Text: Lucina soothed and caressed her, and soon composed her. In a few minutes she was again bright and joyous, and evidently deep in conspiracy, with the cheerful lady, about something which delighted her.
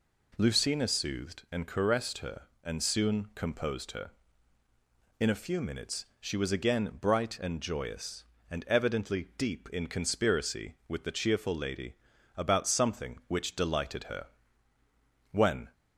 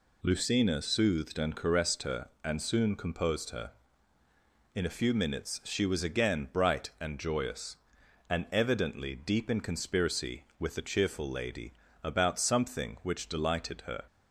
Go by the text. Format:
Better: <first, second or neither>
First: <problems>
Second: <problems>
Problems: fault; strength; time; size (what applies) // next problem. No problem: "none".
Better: second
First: goes on to say "When"; slight; from 15.3 s on; 0.40 s long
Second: none